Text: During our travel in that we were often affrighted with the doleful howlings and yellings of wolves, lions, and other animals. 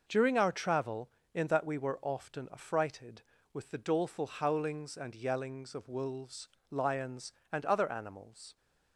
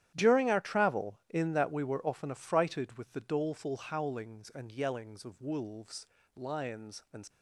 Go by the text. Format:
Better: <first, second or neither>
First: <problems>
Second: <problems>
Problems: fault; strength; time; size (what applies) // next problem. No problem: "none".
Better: first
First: none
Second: starts louder than the rest; strong; until 1.1 s; 11 dB // stops before "other animals"; at 7.2 s